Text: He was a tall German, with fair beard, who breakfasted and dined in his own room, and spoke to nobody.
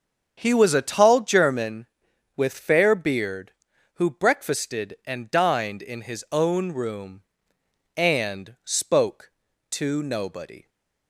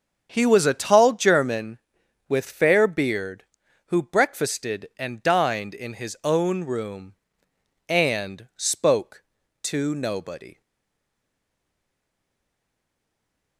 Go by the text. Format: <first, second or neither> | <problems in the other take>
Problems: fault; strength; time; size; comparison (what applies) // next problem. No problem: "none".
first | starts louder than the rest; strong; until 1.3 s; 7.5 dB; strong in the first // stays silent after the last word; strong; from 10.6 s on; 2.9 s long